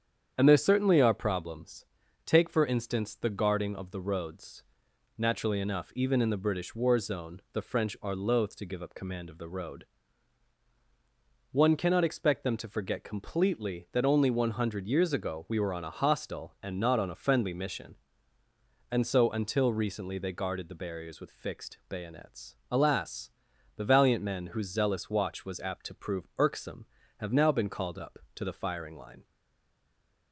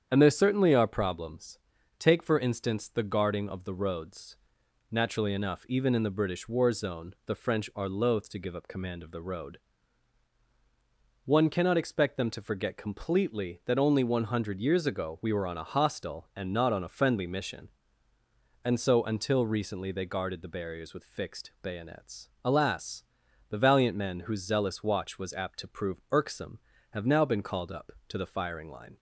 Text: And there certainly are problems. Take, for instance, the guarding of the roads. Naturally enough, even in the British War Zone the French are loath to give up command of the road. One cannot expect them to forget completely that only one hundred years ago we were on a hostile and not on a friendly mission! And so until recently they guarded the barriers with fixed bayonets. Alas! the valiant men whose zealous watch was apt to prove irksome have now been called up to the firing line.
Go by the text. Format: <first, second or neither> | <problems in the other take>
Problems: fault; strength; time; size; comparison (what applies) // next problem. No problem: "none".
second | starts louder than the rest; strong; until 1.3 s; 8.5 dB; strong in the second // stays silent after the last word; from 29.2 s on; 1.1 s long